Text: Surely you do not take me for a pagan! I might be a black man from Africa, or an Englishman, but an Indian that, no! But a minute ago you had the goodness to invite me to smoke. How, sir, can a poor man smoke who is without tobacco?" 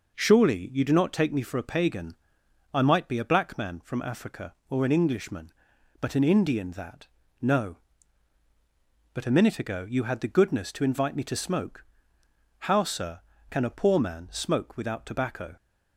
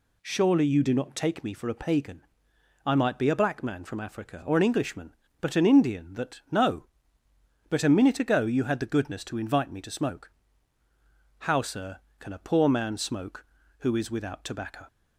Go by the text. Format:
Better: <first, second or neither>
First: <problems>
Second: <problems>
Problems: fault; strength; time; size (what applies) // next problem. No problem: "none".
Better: second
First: skips "who is"; at 14.7 s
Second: none